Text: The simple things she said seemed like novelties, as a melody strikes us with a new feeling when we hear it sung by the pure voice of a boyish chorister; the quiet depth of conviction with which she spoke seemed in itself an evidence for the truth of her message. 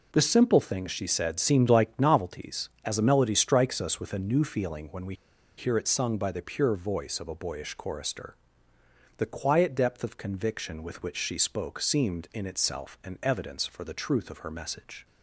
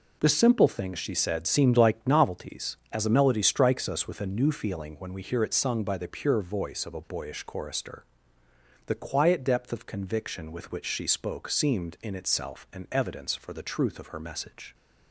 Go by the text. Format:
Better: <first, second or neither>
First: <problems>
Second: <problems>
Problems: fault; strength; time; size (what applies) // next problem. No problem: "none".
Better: second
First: pauses between "we" and "hear"; at 5.1 s; 0.43 s long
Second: none